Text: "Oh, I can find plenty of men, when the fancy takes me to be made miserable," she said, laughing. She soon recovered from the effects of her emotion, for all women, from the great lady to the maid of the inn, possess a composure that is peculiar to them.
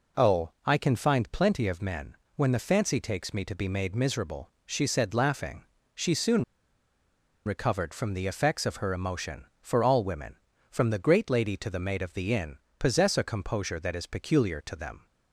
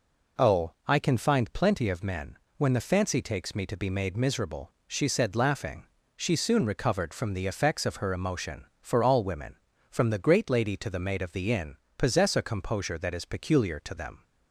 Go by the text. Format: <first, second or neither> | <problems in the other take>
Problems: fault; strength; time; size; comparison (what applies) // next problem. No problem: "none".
second | pauses between "soon" and "recovered"; at 6.4 s; 1.0 s long